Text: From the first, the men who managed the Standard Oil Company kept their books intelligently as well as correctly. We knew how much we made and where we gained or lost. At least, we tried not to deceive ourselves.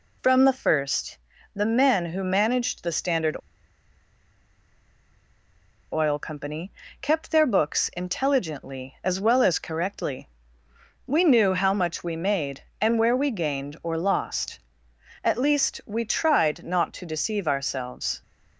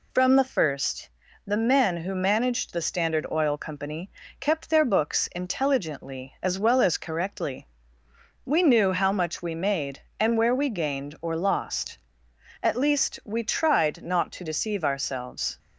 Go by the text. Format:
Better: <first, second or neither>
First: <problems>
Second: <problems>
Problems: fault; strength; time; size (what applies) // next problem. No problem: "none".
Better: second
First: pauses between "Standard" and "Oil"; strong; at 3.3 s; 2.5 s long // pauses between "Company" and "kept"; slight; at 6.7 s; 0.30 s long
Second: pauses between "Company" and "kept"; slight; at 4.1 s; 0.30 s long